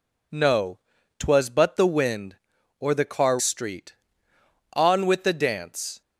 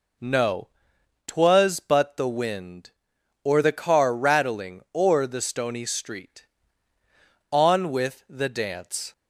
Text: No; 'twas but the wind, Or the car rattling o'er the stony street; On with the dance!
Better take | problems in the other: second | skips "rattling o'er the stony"; at 3.3 s

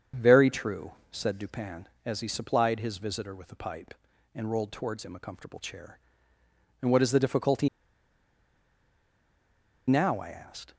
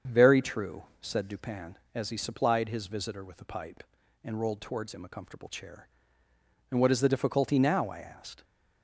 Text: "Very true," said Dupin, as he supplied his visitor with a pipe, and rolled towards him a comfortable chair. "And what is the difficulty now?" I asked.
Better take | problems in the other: second | starts louder than the rest; strong; until 1.3 s; 7 dB; strong in the second // pauses between "difficulty" and "now"; strong; at 7.6 s; 2.1 s long

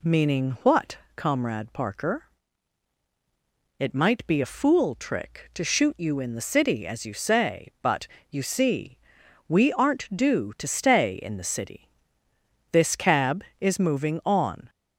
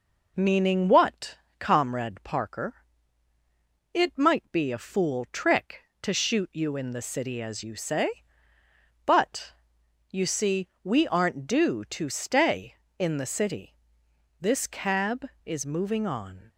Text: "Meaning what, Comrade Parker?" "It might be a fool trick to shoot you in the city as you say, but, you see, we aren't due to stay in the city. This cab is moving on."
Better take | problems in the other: neither | none

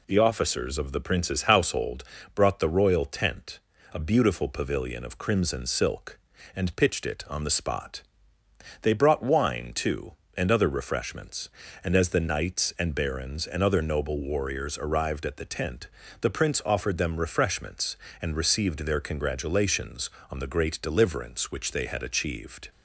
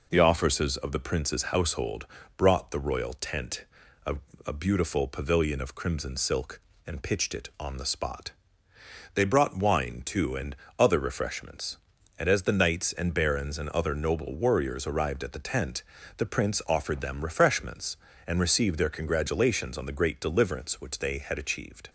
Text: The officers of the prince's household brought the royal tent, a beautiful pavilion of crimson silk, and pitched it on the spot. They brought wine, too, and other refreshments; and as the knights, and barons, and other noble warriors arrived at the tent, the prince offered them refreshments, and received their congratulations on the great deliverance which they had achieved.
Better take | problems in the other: first | pauses between "household" and "brought"; slight; at 2.0 s; 0.28 s long; slight in the first // says "a" twice; at 4.4 s // pauses between "and" and "other"; slight; at 10.5 s; 0.24 s long

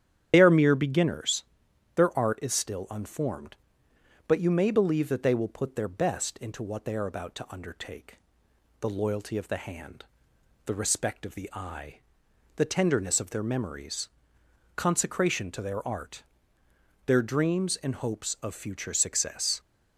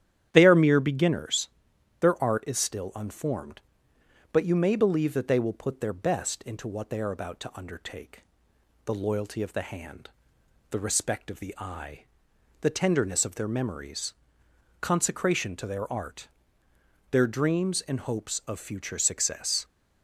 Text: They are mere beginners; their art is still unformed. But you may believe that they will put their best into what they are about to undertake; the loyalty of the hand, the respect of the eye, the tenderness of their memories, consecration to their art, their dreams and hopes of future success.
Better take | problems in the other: second | loses the start of "They"; at 0.3 s; 60 ms // starts louder than the rest; strong; until 1.3 s; 10 dB; strong in the second

